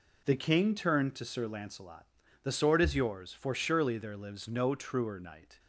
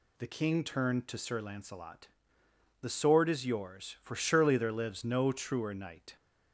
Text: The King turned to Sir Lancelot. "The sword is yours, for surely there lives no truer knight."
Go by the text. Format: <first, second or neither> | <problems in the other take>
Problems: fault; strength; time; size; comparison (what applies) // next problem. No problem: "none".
neither | none